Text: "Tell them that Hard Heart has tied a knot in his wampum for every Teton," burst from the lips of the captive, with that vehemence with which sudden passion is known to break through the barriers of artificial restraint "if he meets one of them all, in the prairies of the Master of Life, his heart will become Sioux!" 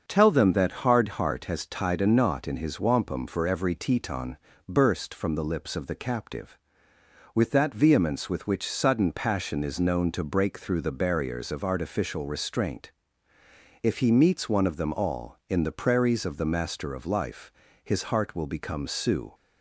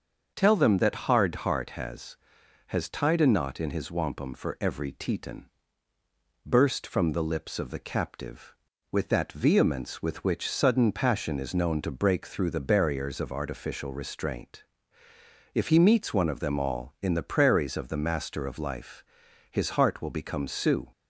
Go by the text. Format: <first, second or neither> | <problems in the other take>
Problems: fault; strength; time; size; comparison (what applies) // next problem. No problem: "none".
first | starts louder than the rest; until 1.3 s; 6.5 dB; also in the first // says "has" twice; at 2.6 s // pauses between "restraint" and "if"; noticeable; at 14.6 s; 0.90 s long; noticeable in the first